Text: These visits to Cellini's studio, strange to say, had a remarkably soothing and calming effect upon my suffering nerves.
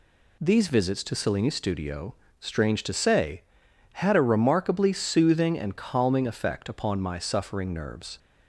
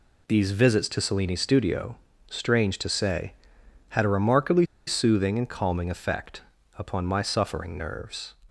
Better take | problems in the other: first | pauses between "remarkably" and "soothing"; slight; at 4.6 s; 0.22 s long // pauses between "effect" and "upon"; slight; at 6.4 s; 0.36 s long

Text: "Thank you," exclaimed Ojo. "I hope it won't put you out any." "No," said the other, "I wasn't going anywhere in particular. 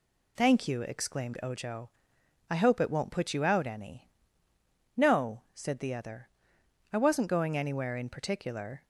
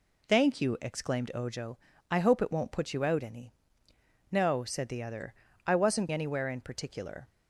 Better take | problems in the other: first | skips "going"; at 6.0 s

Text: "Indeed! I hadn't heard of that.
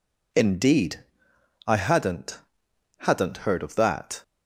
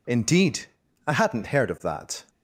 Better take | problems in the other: second | says "hadn't" twice; at 2.9 s

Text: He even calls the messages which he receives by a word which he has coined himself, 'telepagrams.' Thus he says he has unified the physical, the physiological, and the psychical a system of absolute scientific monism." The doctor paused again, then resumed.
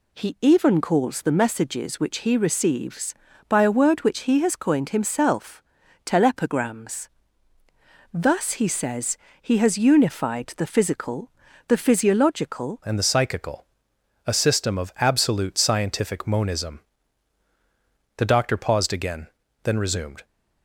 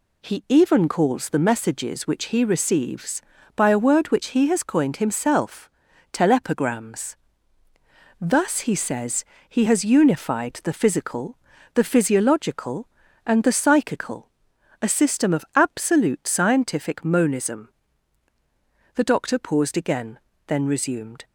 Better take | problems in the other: second | pauses between "says" and "he"; slight; at 9.1 s; 0.24 s long; slight in the second // changes voice at "and"; from 12.8 s on; 7.4 s long // pauses between "psychical" and "a"; noticeable; at 13.6 s; 0.60 s long; noticeable in the second

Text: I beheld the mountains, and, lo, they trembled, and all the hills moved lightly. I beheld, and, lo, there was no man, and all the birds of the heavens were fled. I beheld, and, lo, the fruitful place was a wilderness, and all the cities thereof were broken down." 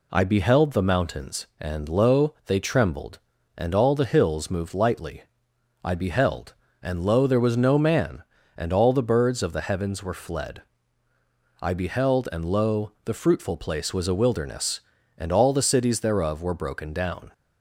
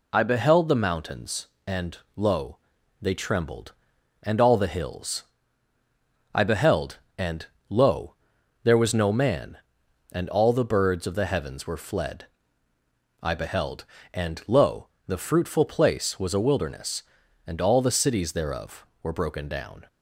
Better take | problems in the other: first | skips "moved lightly"; at 5.7 s

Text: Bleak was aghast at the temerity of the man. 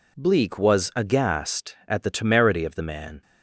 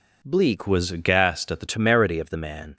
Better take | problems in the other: first | changes voice from "was" to "the"; from 0.6 to 1.6 s; 1.0 s long

